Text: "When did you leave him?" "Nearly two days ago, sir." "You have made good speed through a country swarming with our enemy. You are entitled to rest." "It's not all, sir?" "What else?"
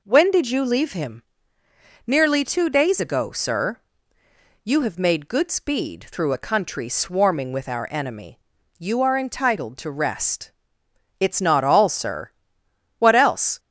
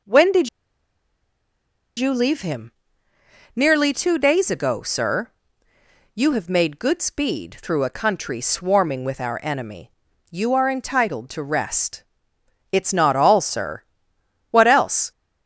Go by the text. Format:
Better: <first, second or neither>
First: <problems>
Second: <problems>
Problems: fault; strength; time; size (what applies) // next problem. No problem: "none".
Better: first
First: none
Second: pauses between "did" and "you"; strong; at 0.4 s; 1.5 s long